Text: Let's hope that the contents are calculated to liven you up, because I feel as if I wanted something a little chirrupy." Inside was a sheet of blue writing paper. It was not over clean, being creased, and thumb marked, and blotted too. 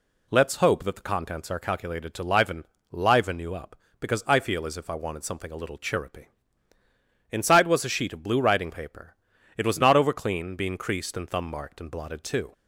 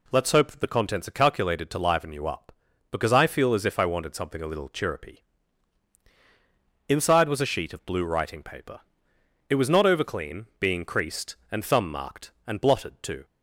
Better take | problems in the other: second | says "liven" twice; at 2.9 s

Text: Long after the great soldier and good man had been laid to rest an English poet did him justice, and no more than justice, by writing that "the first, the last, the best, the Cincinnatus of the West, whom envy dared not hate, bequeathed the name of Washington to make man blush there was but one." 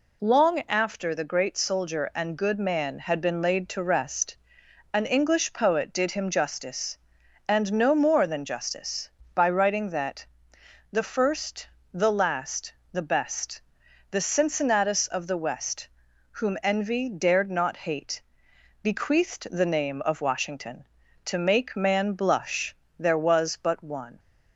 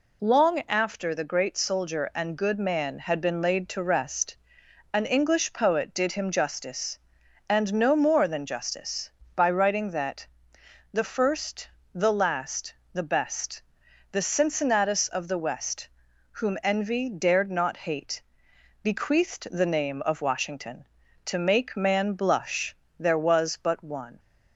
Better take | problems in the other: neither | pauses between "rest" and "an"; noticeable; the same in both // pauses between "that" and "the"; noticeable; the same in both // pauses between "blush" and "there"; slight; the same in both

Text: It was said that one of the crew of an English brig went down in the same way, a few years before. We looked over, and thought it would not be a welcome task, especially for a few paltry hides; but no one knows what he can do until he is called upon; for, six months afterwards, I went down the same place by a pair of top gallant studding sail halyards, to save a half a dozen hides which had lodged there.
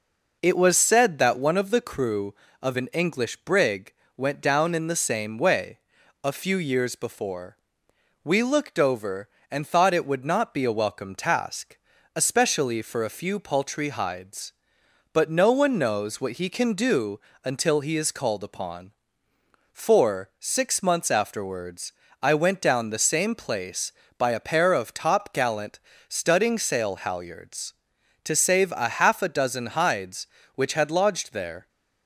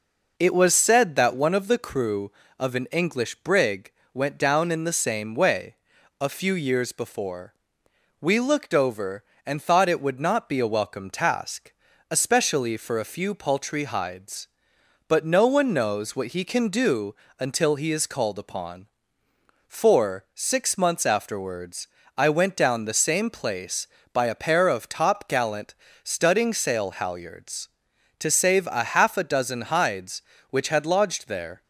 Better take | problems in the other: neither | pauses between "brig" and "went"; slight; the same in both // pauses between "do" and "until"; slight; the same in both // pauses between "gallant" and "studding"; slight; the same in both

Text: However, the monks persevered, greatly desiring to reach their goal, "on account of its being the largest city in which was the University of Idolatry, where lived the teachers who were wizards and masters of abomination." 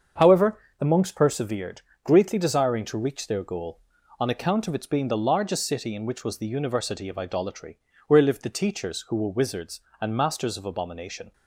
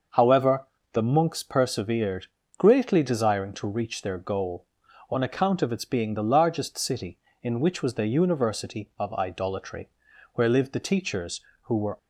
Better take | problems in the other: first | starts louder than the rest; noticeable; until 1.4 s; 6 dB; also in the first // stops before "wizards and masters of abomination"; at 11.9 s

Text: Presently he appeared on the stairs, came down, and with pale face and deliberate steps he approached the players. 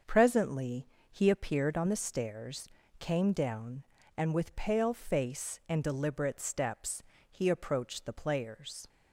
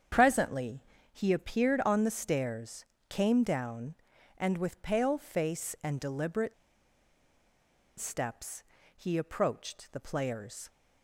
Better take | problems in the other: first | starts louder than the rest; strong; until 1.4 s; 8 dB; also in the first // pauses between "Presently" and "he"; slight; at 0.8 s; 0.28 s long; slight in the first // pauses between "deliberate" and "steps"; strong; at 6.5 s; 1.4 s long // pauses between "steps" and "he"; slight; at 8.6 s; 0.32 s long; slight in the first

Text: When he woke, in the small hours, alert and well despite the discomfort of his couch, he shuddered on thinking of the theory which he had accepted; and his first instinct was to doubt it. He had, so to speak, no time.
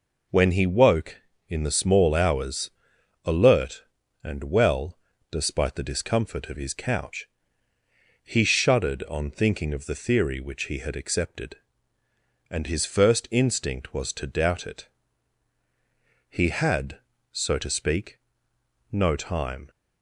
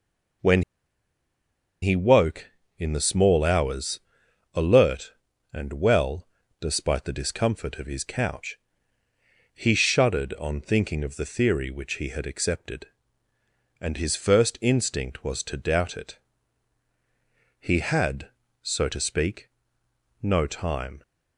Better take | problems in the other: first | pauses between "When" and "he"; at 0.6 s; 1.1 s long // pauses between "well" and "despite"; slight; at 6.2 s; 0.32 s long; slight in the first

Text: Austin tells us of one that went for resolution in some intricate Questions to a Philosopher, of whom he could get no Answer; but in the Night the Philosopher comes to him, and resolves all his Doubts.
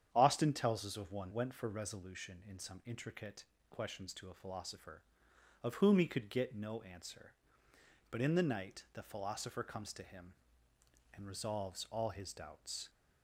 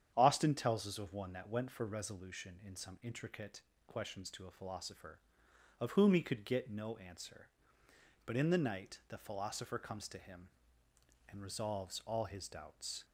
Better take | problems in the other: second | starts louder than the rest; strong; until 1.1 s; 9 dB; strong in the second // skips "that"; at 1.3 s // pauses between "intricate" and "Questions"; slight; at 3.4 s; 0.26 s long; slight in the second

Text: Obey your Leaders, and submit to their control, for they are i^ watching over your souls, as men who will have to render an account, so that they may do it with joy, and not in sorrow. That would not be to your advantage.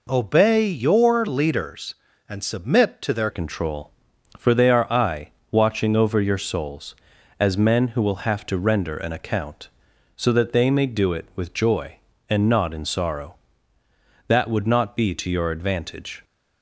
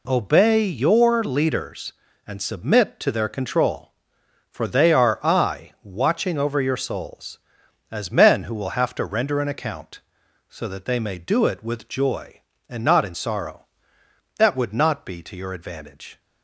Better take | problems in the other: second | changes voice at "control"; from 3.3 s on; 12.9 s long // pauses between "i" and "watching"; slight; at 5.2 s; 0.22 s long

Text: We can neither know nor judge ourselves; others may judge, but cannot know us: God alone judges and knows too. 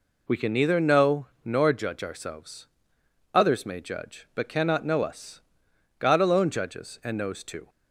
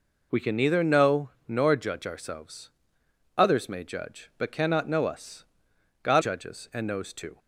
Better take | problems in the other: first | pauses between "know" and "nor"; slight; at 1.3 s; 0.18 s long; slight in the first // skips "alone"; at 6.2 s

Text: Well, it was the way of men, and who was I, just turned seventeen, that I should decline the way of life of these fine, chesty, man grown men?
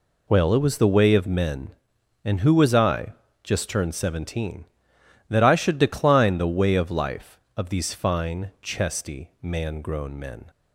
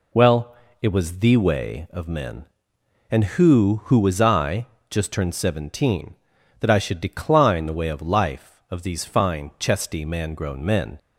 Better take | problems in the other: first | says "who" twice; at 3.8 s

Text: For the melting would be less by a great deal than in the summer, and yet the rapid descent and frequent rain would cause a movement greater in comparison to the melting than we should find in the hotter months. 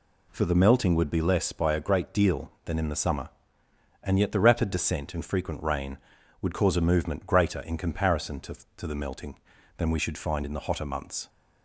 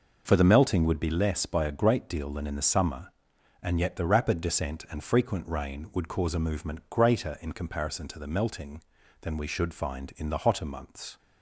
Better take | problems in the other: second | says "to" twice; at 8.7 s

